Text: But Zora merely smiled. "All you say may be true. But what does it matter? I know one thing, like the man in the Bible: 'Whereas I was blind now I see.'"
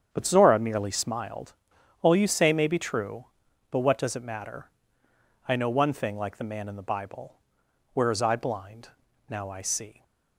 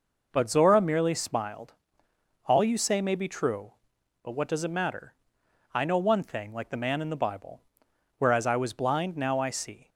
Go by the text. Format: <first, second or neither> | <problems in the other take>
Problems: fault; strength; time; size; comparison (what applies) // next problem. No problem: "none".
second | starts louder than the rest; strong; until 1.1 s; 8 dB // skips "was"; at 8.3 s // pauses between "blind" and "now"; at 8.8 s; 0.40 s long